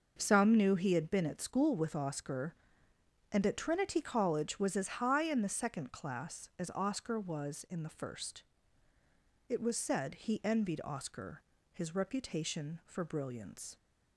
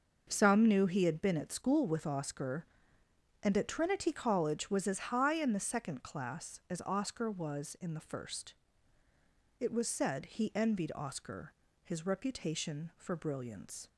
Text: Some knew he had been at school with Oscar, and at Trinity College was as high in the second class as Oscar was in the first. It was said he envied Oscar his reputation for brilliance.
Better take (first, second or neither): neither